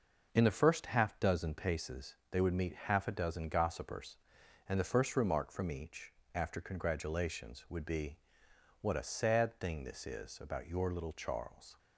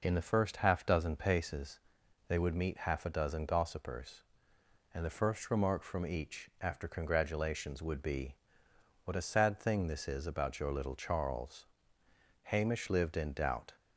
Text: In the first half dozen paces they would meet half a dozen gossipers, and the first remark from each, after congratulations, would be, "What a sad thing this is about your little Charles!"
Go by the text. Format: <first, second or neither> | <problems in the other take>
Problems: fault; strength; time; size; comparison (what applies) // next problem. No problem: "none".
first | pauses between "paces" and "they"; noticeable; at 1.7 s; 0.48 s long; slight in the first // goes on to say "Hamish lived in doubt"; from 12.4 s on; 1.3 s long